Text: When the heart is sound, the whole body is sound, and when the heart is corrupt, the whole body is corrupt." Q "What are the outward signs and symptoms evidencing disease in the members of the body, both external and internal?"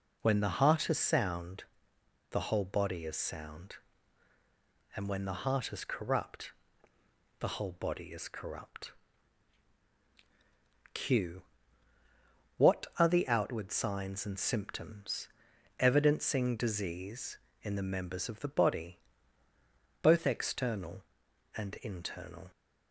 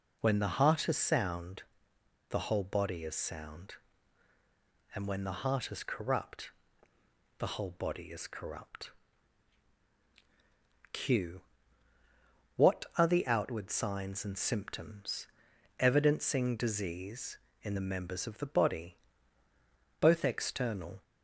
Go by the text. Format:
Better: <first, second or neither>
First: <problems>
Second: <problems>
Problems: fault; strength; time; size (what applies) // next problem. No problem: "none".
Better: first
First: pauses between "Q" and "What"; at 11.4 s; 1.1 s long // pauses between "symptoms" and "evidencing"; noticeable; at 15.2 s; 0.48 s long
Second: pauses between "Q" and "What"; at 11.4 s; 1.1 s long // pauses between "symptoms" and "evidencing"; noticeable; at 15.2 s; 0.50 s long // stops before "and internal"; at 21.0 s